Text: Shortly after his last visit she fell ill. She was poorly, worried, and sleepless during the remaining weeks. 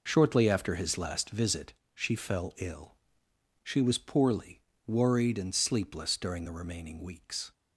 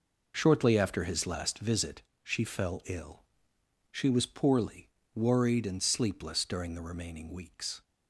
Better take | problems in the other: neither | pauses between "visit" and "she"; slight; the same in both

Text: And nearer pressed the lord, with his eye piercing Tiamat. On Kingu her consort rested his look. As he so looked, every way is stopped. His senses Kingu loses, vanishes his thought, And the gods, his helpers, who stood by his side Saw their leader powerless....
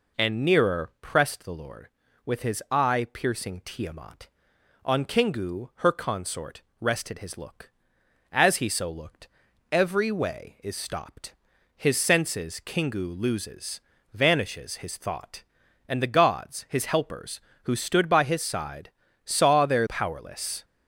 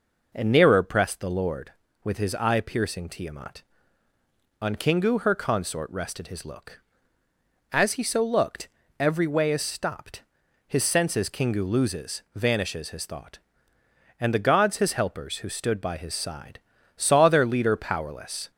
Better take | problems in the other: second | pauses between "consort" and "rested"; slight; at 6.6 s; 0.18 s long // pauses between "side" and "Saw"; slight; at 18.9 s; 0.34 s long; slight in the second // skips "leader"; at 19.8 s

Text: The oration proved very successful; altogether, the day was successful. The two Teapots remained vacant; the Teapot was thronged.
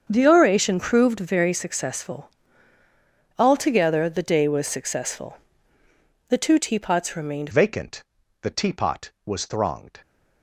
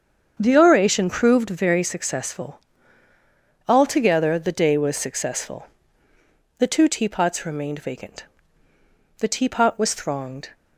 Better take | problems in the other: second | starts louder than the rest; until 1.1 s; 7 dB; also in the second // changes voice at "vacant"; from 7.5 s on; 2.5 s long

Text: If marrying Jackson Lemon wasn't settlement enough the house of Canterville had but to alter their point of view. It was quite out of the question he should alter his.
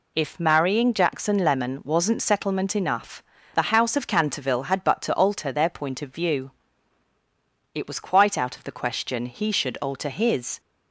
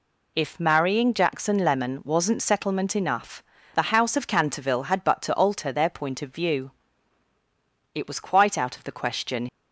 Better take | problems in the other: first | pauses between "enough" and "the"; slight; at 3.4 s; 0.32 s long; slight in the first // stops before "he should alter his"; at 9.4 s

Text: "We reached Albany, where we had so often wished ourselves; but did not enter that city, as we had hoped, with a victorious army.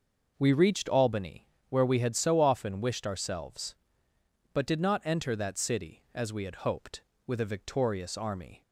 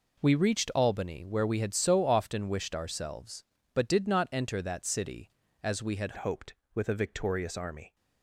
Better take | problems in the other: first | changes voice at "hoped"; from 6.1 s on; 1.8 s long

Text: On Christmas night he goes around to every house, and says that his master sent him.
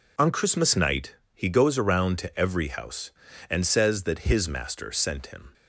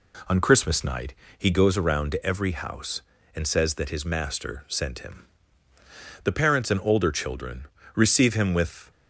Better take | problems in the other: first | pauses between "night" and "he"; slight; at 1.1 s; 0.24 s long; slight in the first // goes on to say "The parents and older children receive him with"; strong; from 6.2 s on; 2.6 s long

